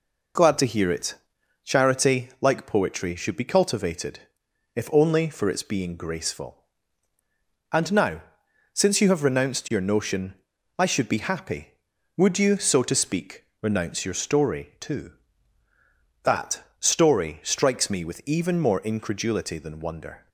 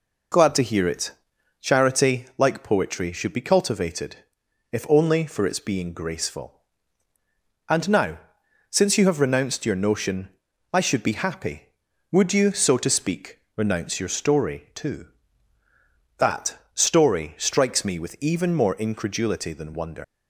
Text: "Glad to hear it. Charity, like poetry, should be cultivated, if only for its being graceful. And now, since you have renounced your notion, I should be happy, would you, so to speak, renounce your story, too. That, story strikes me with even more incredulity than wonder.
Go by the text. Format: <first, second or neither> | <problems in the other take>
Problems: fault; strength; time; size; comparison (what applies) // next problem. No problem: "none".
first | leaves "wonder" unfinished; at 20.0 s; 175 ms